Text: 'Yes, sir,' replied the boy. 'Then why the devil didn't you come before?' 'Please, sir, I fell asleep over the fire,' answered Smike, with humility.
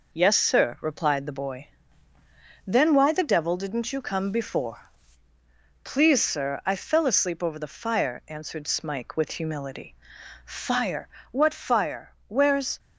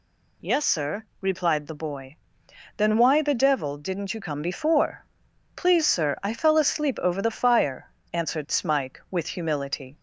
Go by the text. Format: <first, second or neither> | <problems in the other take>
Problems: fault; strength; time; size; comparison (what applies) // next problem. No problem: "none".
second | goes on to say "Fire what fire Where's"; strong; from 10.4 s on; 2.3 s long